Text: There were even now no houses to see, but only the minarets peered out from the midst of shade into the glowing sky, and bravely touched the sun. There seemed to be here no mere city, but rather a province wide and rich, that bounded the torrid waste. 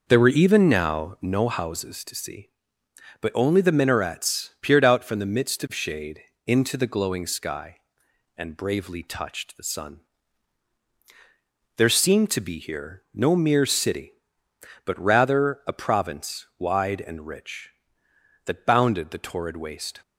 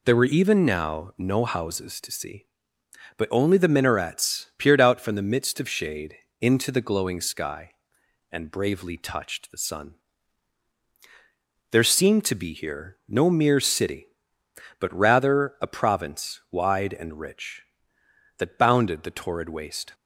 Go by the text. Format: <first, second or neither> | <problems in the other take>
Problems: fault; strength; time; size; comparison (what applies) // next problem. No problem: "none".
second | starts louder than the rest; noticeable; until 1.5 s; 5 dB // pauses between "shade" and "into"; slight; at 6.2 s; 0.24 s long; slight in the second